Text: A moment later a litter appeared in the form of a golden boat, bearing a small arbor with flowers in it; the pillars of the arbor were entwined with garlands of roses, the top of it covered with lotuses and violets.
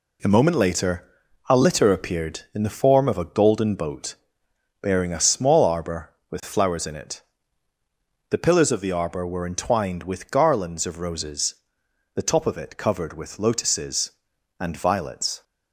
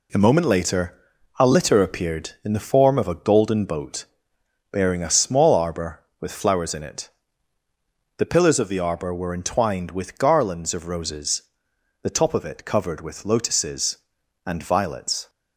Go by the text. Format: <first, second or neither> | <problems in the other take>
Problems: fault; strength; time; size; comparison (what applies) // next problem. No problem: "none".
neither | pauses between "later" and "a"; noticeable; the same in both